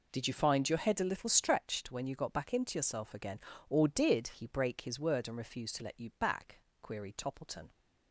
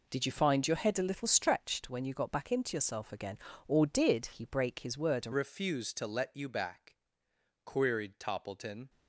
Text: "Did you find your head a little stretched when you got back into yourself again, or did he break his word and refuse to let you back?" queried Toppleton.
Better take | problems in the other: first | changes voice at "refuse"; from 5.3 s on; 3.5 s long

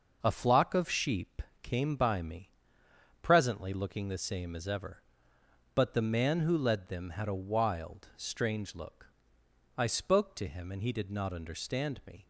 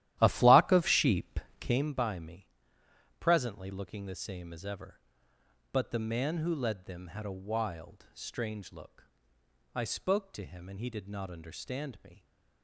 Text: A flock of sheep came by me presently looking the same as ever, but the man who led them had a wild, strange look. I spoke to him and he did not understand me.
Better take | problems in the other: first | starts louder than the rest; strong; until 1.9 s; 13.5 dB // pauses between "sheep" and "came"; slight; at 1.3 s; 0.22 s long; slight in the first // pauses between "me" and "presently"; noticeable; at 2.4 s; 0.72 s long; noticeable in the first

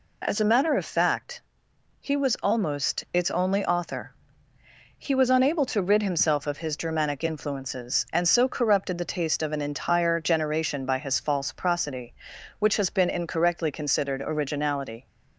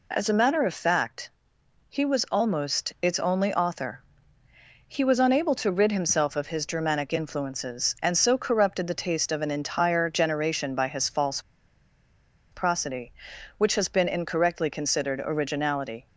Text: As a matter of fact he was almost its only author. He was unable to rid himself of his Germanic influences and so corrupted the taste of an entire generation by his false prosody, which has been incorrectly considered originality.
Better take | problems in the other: first | pauses between "fact" and "he"; noticeable; at 1.2 s; 0.58 s long; noticeable in the first // pauses between "false" and "prosody"; at 11.3 s; 1.1 s long

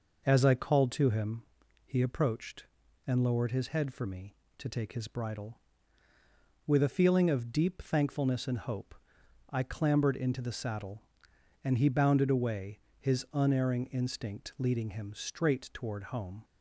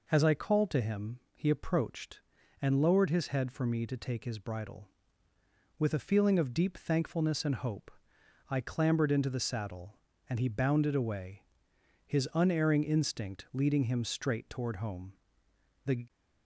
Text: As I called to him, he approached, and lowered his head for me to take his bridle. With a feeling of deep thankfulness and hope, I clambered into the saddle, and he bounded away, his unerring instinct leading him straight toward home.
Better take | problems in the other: first | goes on to say "The"; slight; from 15.8 s on; 0.20 s long

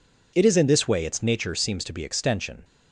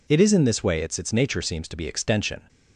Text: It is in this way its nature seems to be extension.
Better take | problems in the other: first | says "its" twice; at 0.9 s

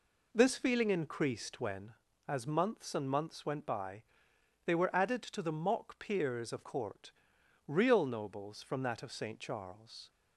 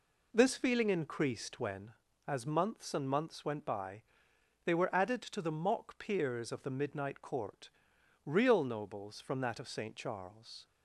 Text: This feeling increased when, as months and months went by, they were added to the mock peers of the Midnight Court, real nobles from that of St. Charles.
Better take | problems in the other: second | skips "the Midnight"; at 6.6 s

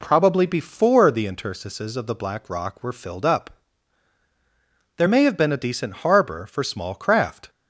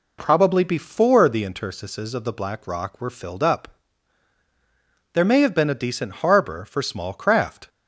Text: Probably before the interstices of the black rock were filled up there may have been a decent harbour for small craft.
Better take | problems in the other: neither | pauses between "up" and "there"; strong; the same in both

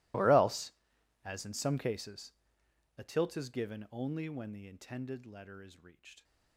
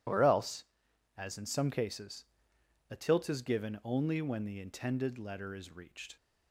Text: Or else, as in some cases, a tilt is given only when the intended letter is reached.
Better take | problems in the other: second | gets quieter; strong; throughout; 23.5 dB

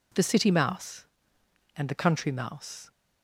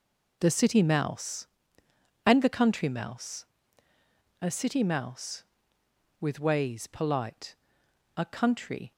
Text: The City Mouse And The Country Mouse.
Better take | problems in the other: first | goes on to say "A City Mouse with ways polite A Country"; strong; from 4.3 s on; 4.5 s long

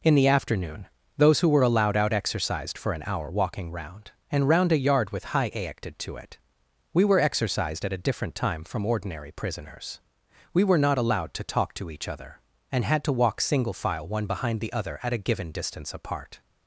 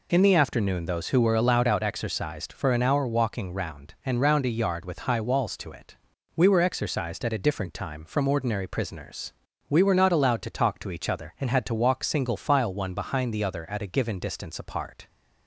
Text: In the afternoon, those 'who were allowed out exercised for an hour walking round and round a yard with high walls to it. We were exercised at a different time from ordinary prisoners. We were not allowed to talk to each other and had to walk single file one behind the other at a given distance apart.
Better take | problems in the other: second | says "aected" for "walls"; at 5.5 s

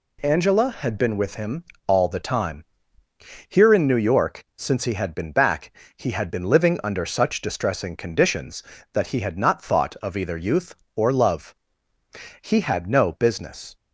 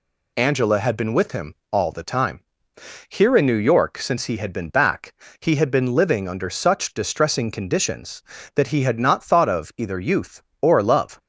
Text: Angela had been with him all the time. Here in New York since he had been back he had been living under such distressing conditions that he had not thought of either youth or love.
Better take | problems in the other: second | pauses between "him" and "all"; slight; at 1.6 s; 0.24 s long; slight in the second // pauses between "back" and "he"; slight; at 5.7 s; 0.24 s long; slight in the second // goes on to say "He had no business"; from 12.4 s on; 1.3 s long

